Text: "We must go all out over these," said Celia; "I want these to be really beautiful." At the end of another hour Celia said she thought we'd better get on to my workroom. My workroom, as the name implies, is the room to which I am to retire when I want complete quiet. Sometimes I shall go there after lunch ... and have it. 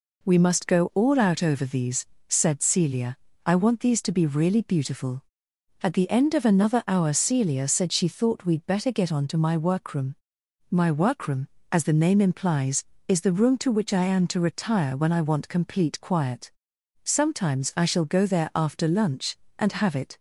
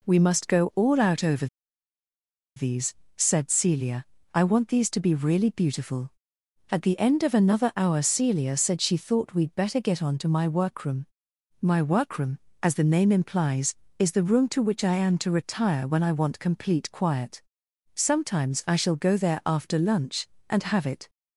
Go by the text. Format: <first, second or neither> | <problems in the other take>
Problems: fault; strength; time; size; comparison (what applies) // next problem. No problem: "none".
first | pauses between "over" and "these"; at 1.4 s; 1.1 s long